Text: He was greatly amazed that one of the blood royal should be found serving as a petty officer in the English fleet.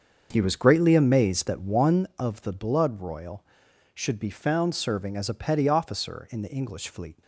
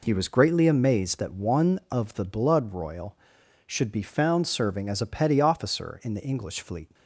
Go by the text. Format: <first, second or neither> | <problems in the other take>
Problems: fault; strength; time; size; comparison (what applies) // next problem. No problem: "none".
second | starts louder than the rest; until 2.0 s; 7 dB